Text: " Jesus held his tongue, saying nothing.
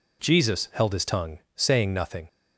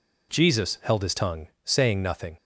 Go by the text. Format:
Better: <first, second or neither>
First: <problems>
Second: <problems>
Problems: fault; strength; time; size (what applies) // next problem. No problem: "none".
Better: neither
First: none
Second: none